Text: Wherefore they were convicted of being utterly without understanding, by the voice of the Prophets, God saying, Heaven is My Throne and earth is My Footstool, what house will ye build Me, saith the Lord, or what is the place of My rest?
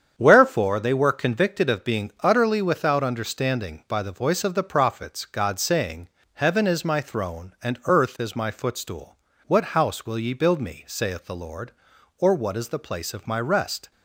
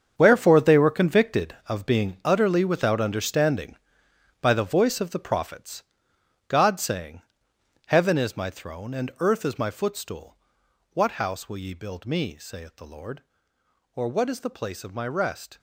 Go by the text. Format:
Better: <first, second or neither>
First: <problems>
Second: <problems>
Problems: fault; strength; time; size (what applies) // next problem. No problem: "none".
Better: first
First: starts louder than the rest; strong; until 1.1 s; 8 dB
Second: gets quieter; strong; throughout; 13 dB // starts louder than the rest; strong; until 1.1 s; 7 dB